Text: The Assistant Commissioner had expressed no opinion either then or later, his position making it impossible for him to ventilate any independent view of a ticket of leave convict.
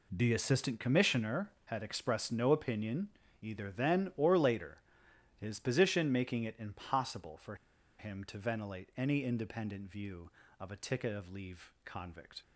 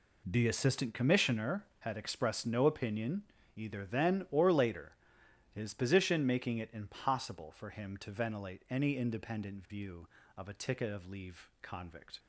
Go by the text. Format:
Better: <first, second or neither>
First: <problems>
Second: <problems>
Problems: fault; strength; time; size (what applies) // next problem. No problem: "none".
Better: second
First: pauses between "opinion" and "either"; slight; at 3.1 s; 0.30 s long // pauses between "for" and "him"; at 7.5 s; 0.44 s long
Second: pauses between "opinion" and "either"; slight; at 3.2 s; 0.30 s long